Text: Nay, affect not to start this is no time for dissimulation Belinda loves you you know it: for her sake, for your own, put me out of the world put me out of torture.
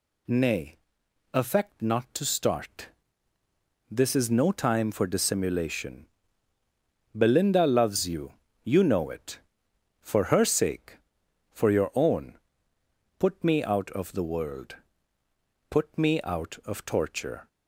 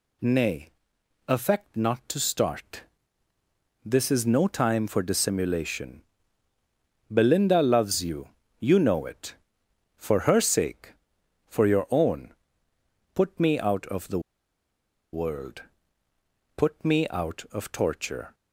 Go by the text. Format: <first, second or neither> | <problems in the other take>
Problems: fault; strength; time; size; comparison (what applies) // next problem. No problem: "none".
first | pauses between "start" and "this"; at 2.8 s; 1.0 s long; also in the first // pauses between "dissimulation" and "Belinda"; at 6.0 s; 1.1 s long; also in the first // pauses between "you" and "you"; slight; at 8.2 s; 0.30 s long; slight in the first // pauses between "the" and "world"; noticeable; at 14.1 s; 0.93 s long // pauses between "world" and "put"; noticeable; at 15.6 s; 0.94 s long; noticeable in the first